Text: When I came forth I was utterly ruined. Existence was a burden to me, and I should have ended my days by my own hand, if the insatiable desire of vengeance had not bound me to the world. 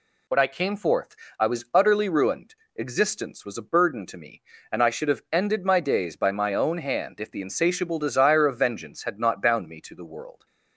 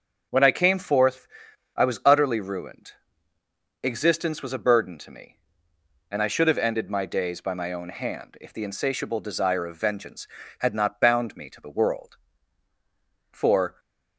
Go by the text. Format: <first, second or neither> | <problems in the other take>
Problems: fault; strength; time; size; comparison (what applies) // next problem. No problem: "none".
first | starts louder than the rest; until 1.7 s; 6.5 dB // pauses between "forth" and "I"; noticeable; at 1.2 s; 0.48 s long; slight in the first // goes on to say "For"; slight; from 13.3 s on; 0.48 s long